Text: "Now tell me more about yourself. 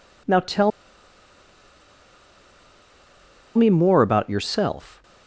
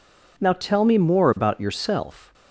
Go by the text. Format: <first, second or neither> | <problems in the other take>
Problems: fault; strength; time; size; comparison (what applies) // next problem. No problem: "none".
second | pauses between "tell" and "me"; strong; at 0.7 s; 2.8 s long